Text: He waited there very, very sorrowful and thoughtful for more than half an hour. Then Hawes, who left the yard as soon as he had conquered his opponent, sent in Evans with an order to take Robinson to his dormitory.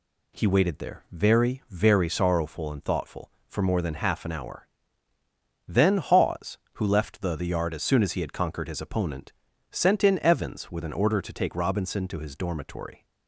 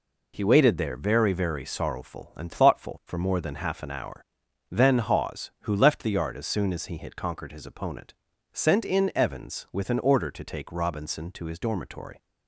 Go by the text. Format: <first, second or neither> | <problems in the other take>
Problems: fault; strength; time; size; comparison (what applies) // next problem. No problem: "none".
second | says "the" twice; at 7.3 s